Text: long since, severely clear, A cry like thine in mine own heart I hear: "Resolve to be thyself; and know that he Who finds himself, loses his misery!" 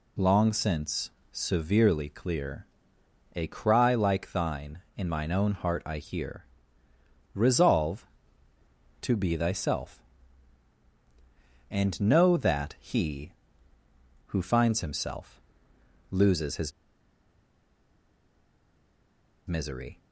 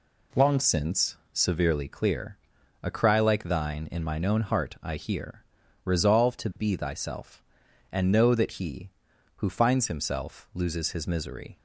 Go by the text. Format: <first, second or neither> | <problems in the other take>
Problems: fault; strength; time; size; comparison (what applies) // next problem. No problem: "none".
second | pauses between "his" and "misery"; strong; at 16.7 s; 2.7 s long